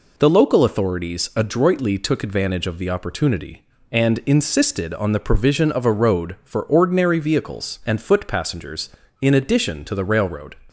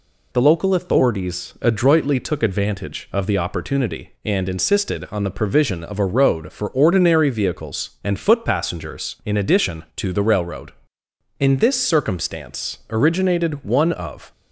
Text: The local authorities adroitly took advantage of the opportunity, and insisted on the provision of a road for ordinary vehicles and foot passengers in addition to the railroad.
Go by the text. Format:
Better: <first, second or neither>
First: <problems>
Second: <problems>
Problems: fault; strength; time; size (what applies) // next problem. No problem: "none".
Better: first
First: none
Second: goes on to say "In this circumstance originated one of"; strong; from 11.3 s on; 2.9 s long